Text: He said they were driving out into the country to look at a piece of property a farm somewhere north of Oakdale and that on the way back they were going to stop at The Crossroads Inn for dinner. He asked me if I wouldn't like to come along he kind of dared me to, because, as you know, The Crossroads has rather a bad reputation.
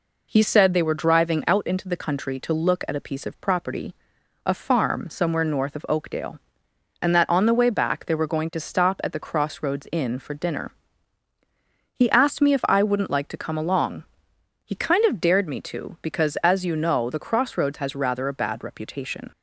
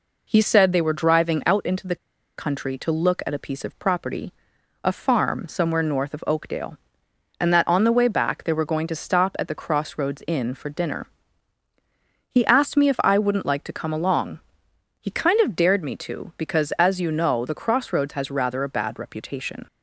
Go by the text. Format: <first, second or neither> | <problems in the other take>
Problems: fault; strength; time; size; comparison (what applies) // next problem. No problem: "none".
first | pauses between "the" and "country"; at 1.9 s; 0.42 s long // pauses between "property" and "a"; noticeable; at 4.3 s; 0.50 s long; noticeable in the first // pauses between "along" and "he"; noticeable; at 14.4 s; 0.58 s long; noticeable in the first